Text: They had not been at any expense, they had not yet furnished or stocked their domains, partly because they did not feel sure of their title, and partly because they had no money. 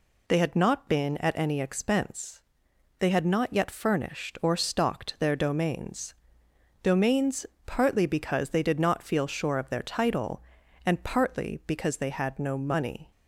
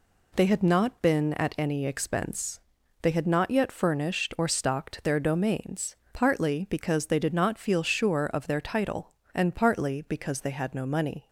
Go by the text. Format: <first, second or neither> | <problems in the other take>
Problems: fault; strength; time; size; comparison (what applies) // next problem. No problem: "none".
second | says "domains" twice; at 6.8 s